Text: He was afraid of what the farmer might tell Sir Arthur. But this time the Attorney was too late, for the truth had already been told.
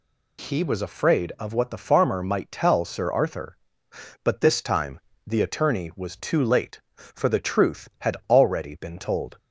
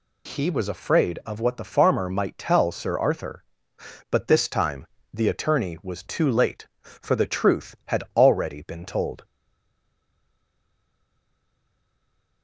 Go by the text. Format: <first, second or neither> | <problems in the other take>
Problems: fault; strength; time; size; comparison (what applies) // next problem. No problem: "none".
first | pauses between "time" and "the"; slight; at 4.8 s; 0.30 s long; slight in the first // stays silent after the last word; strong; from 9.2 s on; 3.2 s long